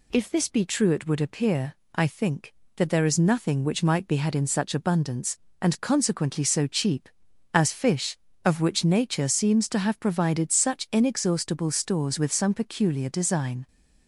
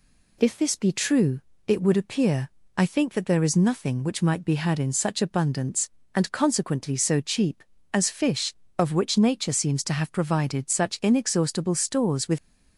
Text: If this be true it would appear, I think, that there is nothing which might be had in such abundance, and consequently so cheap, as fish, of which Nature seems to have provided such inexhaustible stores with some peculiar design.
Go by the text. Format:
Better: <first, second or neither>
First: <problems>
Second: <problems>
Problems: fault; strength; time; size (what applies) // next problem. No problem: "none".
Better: first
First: none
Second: pauses between "true" and "it"; slight; at 1.4 s; 0.26 s long // stops before "some peculiar design"; at 12.3 s